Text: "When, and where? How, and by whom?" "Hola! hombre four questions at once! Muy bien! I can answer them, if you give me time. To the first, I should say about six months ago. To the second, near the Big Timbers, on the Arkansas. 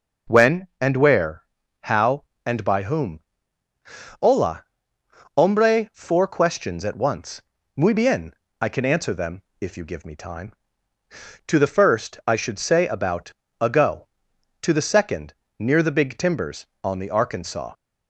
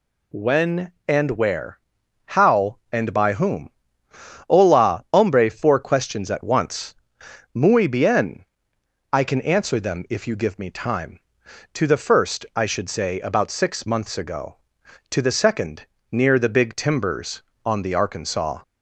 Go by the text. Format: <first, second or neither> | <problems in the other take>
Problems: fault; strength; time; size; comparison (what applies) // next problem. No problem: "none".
second | skips "six months"; at 13.4 s